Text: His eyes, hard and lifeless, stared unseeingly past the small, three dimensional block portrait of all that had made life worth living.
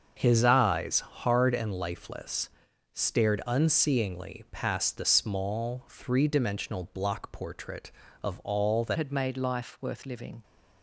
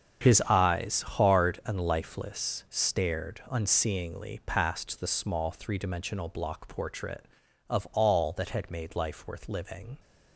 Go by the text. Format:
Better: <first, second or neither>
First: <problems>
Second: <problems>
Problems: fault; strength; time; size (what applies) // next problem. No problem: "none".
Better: second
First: starts louder than the rest; until 1.1 s; 6.5 dB // changes voice at "had"; from 8.9 s on; 1.5 s long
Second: starts louder than the rest; strong; until 1.3 s; 7 dB